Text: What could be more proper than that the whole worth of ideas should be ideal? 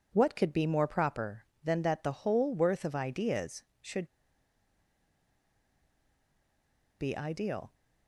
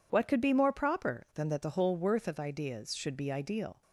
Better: second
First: pauses between "should" and "be"; strong; at 4.0 s; 2.9 s long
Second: none

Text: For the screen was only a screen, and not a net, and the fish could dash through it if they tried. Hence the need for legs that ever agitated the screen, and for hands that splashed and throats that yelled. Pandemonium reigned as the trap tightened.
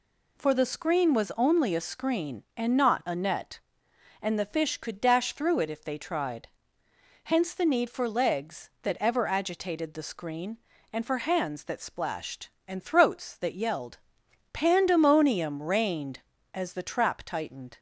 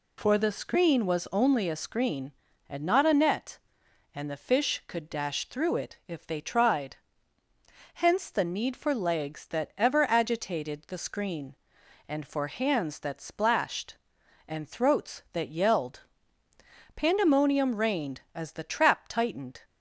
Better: neither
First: none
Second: none

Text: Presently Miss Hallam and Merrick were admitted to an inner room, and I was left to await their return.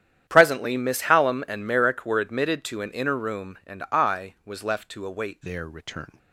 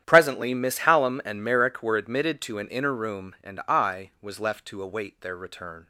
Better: second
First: starts louder than the rest; strong; until 1.2 s; 10.5 dB // changes voice at "their"; from 5.4 s on; 0.7 s long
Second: starts louder than the rest; strong; until 1.0 s; 10.5 dB

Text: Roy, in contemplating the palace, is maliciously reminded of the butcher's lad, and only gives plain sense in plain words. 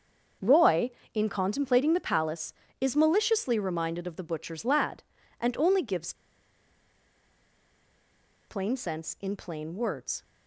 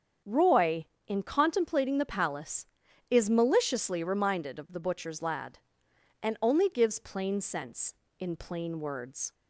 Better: second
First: starts louder than the rest; until 1.6 s; 7 dB // pauses between "gives" and "plain"; strong; at 6.1 s; 2.3 s long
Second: starts louder than the rest; strong; until 1.4 s; 7.5 dB

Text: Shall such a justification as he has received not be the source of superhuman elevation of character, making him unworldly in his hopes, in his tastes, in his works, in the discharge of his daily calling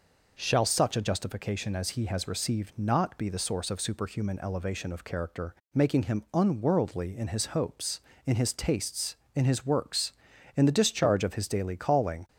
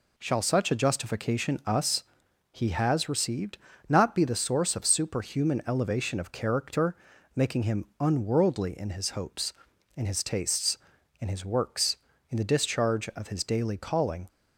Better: first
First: none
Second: says "us" for "as"; at 1.6 s // pauses between "received" and "not"; slight; at 3.5 s; 0.30 s long // pauses between "him" and "unworldly"; slight; at 7.8 s; 0.16 s long

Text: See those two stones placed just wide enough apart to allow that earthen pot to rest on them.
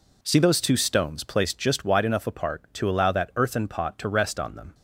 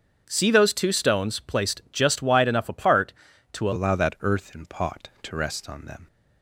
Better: first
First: none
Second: starts louder than the rest; until 1.2 s; 7 dB // changes voice at "allow"; from 3.7 s on; 2.3 s long

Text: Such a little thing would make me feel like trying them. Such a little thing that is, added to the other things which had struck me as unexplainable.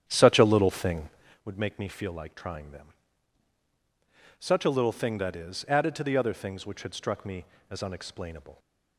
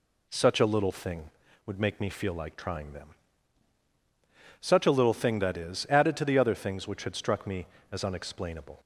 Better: second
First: starts louder than the rest; strong; until 1.5 s; 9.5 dB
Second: none

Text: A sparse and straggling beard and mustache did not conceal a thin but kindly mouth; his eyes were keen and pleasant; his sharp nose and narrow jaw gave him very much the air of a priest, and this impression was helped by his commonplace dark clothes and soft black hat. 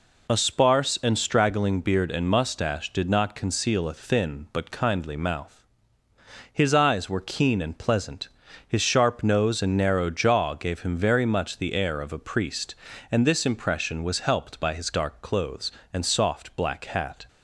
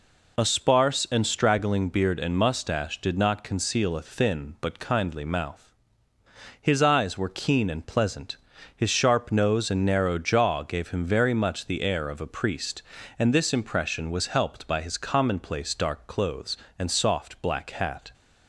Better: second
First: skips "commonplace"; at 14.9 s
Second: none

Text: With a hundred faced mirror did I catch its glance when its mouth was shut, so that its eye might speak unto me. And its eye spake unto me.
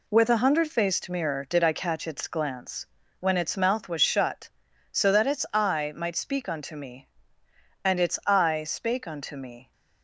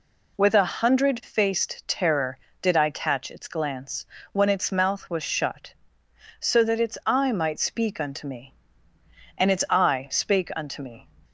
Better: first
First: pauses between "glance" and "when"; slight; at 2.8 s; 0.32 s long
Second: says "terror" for "mirror"; at 1.8 s // pauses between "glance" and "when"; slight; at 4.0 s; 0.28 s long

